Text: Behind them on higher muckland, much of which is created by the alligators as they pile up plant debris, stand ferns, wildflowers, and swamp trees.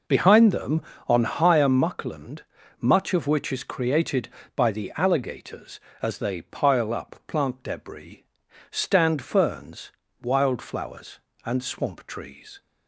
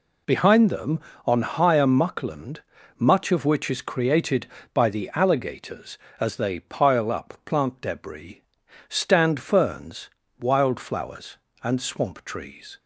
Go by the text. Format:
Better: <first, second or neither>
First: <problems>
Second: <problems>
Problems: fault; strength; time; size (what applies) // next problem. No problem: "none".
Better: second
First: starts louder than the rest; noticeable; until 1.7 s; 5 dB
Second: none